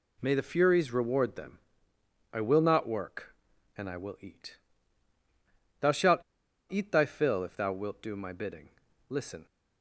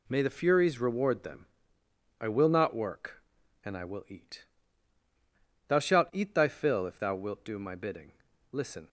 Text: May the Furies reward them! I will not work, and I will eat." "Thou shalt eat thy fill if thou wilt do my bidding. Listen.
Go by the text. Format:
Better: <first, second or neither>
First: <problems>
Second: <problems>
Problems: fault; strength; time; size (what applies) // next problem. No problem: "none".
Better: second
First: pauses between "shalt" and "eat"; noticeable; at 6.1 s; 0.52 s long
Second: none